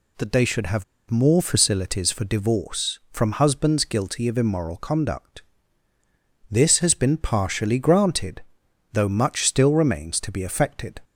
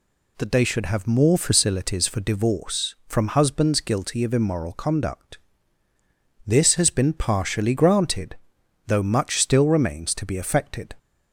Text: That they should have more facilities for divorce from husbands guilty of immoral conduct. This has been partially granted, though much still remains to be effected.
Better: second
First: pauses between "have" and "more"; slight; at 0.8 s; 0.26 s long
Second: none

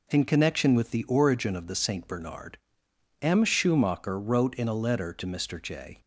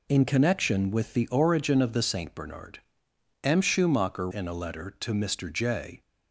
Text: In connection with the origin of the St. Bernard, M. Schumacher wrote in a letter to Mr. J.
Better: first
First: none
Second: skips "wrote"; at 4.3 s

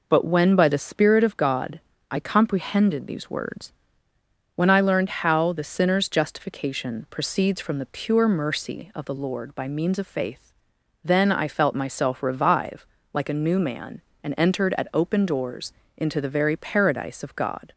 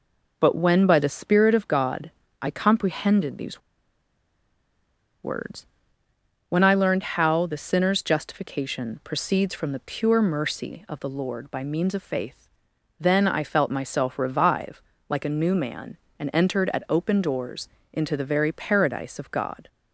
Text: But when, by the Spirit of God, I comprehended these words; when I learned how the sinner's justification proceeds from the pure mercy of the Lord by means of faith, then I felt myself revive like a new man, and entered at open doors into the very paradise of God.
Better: first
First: pauses between "revive" and "like"; slight; at 12.8 s; 0.26 s long // pauses between "doors" and "into"; slight; at 15.7 s; 0.24 s long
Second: pauses between "these" and "words"; strong; at 3.5 s; 1.6 s long // pauses between "revive" and "like"; slight; at 14.8 s; 0.26 s long // pauses between "doors" and "into"; slight; at 17.6 s; 0.24 s long

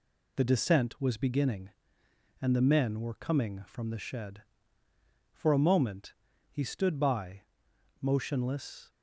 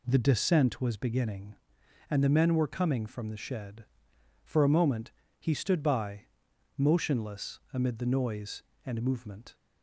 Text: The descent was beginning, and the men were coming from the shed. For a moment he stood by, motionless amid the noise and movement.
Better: second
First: pauses between "moment" and "he"; at 6.1 s; 0.38 s long // stops before "amid the noise and movement"; at 8.8 s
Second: pauses between "moment" and "he"; slight; at 5.1 s; 0.28 s long

